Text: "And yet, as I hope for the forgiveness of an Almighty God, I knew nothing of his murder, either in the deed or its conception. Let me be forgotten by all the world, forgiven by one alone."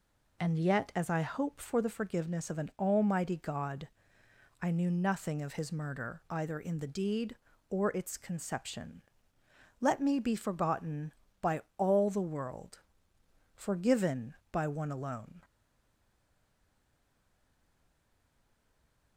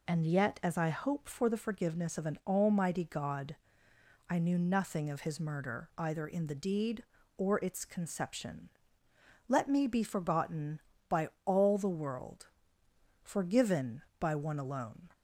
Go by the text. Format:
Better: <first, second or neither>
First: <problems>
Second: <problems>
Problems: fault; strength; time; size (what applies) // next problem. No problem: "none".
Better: second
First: pauses between "by" and "all"; slight; at 11.6 s; 0.16 s long // stays silent after the last word; strong; from 15.4 s on; 3.7 s long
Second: pauses between "by" and "all"; slight; at 11.2 s; 0.16 s long